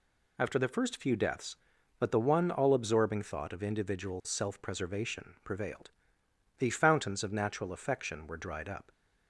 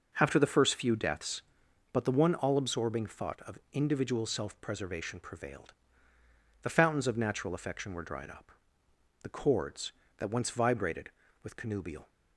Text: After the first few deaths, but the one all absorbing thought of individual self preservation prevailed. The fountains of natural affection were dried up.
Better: first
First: none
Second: goes on to say "The chords that once vibrated with connubial"; strong; from 9.2 s on; 2.8 s long

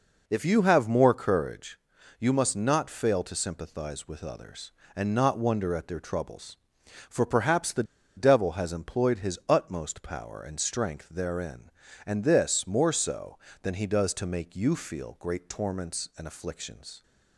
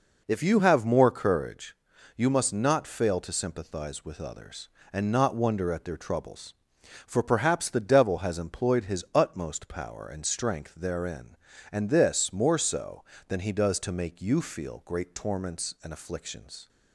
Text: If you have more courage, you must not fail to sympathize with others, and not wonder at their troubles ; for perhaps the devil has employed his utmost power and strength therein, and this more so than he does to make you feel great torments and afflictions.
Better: second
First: pauses between "the" and "devil"; slight; at 7.8 s; 0.33 s long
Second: none

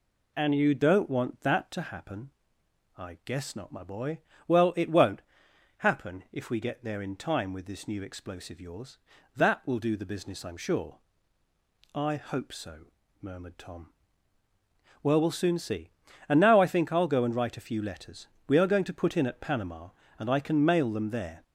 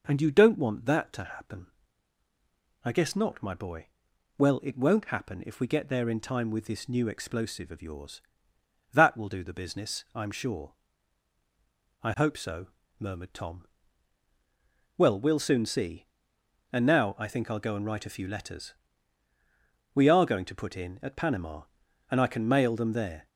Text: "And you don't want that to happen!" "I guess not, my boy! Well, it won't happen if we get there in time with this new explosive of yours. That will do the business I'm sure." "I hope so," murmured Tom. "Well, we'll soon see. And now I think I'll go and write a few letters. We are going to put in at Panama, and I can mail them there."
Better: second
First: pauses between "won't" and "happen"; noticeable; at 5.2 s; 0.56 s long // skips "of"; at 8.5 s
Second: none

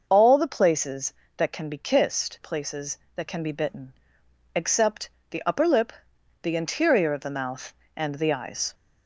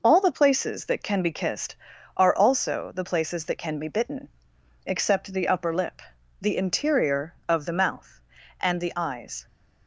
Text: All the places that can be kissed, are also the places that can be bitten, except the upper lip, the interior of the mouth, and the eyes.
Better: second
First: starts louder than the rest; noticeable; until 1.0 s; 6 dB // skips "are also the"; at 2.4 s // pauses between "except" and "the"; slight; at 5.0 s; 0.20 s long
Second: none

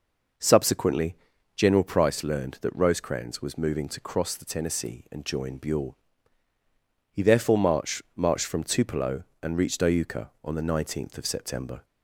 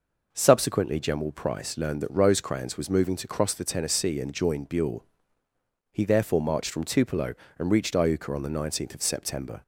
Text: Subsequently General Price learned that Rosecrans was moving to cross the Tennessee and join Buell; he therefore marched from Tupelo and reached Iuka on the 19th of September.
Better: second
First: pauses between "Subsequently" and "General"; at 1.1 s; 0.40 s long // says "marched" twice; at 8.1 s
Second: none

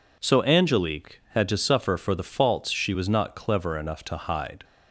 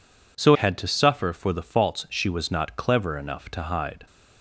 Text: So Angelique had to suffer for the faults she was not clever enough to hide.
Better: first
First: none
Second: skips "Angelique"; at 0.5 s

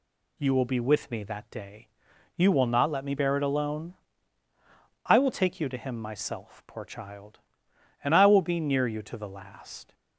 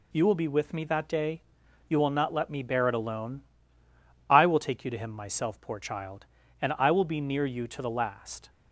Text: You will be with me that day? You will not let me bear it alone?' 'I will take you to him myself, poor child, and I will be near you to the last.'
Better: neither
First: none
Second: none

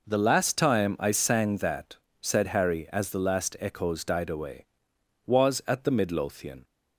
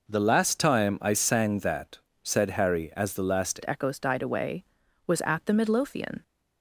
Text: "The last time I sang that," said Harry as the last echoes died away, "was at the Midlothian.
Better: first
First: none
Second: changes voice at "echoes"; from 3.6 s on; 2.6 s long

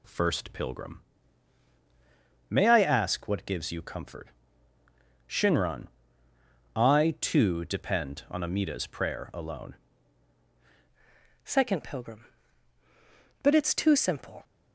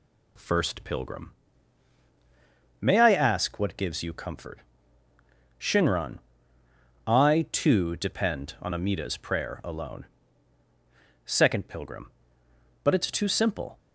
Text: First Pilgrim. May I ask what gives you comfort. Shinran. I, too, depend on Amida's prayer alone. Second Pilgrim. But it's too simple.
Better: second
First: changes voice at "Second"; from 11.4 s on; 3.0 s long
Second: none

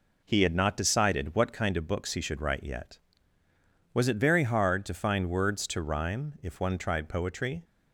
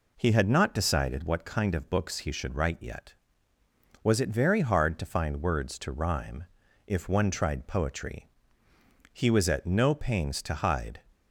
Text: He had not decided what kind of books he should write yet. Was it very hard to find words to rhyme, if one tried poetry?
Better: first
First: none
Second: goes on to say "He was at no pains to hide"; strong; from 9.1 s on; 1.8 s long

